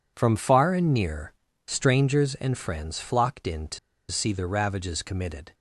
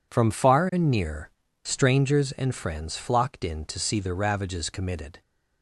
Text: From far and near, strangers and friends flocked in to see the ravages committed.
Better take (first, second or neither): second